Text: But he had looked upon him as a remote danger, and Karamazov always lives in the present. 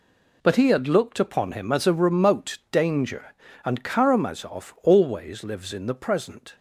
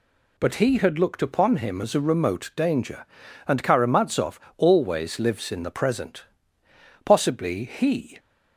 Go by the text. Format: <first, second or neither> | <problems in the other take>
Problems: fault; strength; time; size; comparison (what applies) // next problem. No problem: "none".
first | pauses between "Karamazov" and "always"; slight; at 4.3 s; 0.18 s long // goes on to say "Possibly he"; noticeable; from 7.0 s on; 1.1 s long